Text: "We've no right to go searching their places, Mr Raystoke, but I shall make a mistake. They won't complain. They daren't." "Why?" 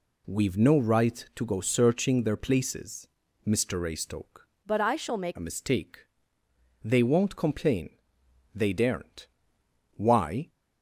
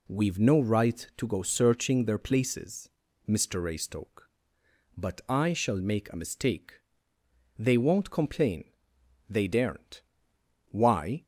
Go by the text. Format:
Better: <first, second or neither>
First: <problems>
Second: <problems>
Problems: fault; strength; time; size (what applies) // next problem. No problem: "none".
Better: second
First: changes voice from "but" to "make"; from 4.6 to 5.3 s; 0.7 s long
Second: none